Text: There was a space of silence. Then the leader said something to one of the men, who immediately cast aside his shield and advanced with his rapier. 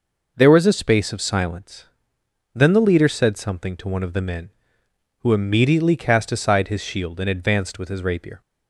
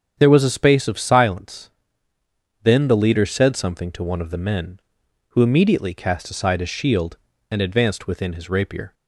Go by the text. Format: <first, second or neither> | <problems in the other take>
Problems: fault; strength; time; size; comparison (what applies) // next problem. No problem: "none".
first | starts louder than the rest; strong; until 1.2 s; 8 dB // says "within" for "with"; at 8.0 s